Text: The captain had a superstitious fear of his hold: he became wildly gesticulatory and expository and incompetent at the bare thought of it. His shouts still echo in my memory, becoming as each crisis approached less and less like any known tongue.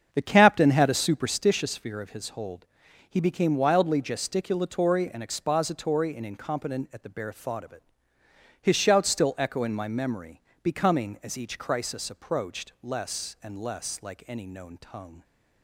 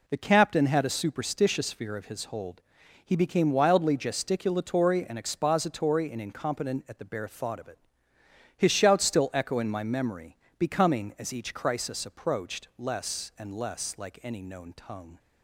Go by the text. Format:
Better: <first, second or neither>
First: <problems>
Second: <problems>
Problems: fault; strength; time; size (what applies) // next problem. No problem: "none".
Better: second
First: starts louder than the rest; strong; until 1.6 s; 7.5 dB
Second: none